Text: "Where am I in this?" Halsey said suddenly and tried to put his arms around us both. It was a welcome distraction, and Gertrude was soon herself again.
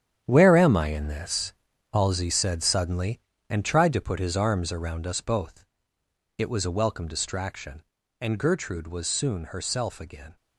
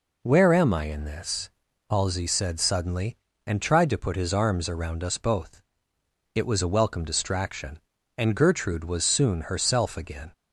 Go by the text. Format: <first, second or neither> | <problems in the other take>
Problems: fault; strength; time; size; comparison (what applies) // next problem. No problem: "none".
second | gets quieter; strong; throughout; 11 dB